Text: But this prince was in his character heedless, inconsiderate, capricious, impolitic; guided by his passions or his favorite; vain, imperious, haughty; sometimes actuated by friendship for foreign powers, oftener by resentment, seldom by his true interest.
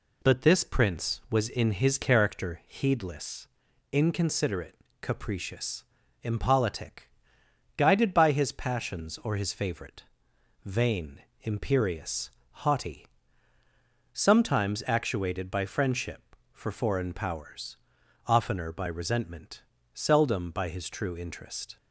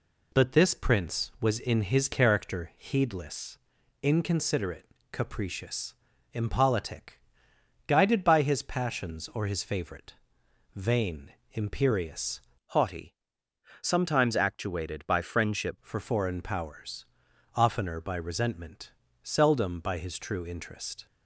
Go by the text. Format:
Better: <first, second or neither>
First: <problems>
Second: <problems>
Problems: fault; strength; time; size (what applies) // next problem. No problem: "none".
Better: first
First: none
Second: changes voice from "haughty" to "friendship"; from 12.6 to 15.7 s; 3.1 s long